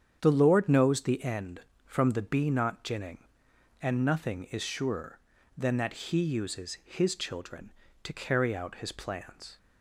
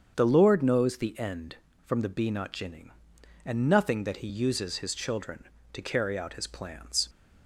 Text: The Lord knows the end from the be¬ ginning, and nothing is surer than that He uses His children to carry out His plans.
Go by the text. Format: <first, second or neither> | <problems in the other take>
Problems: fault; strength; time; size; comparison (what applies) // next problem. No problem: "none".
first | starts louder than the rest; strong; until 1.1 s; 7.5 dB; strong in the first // skips "is surer than"; at 4.0 s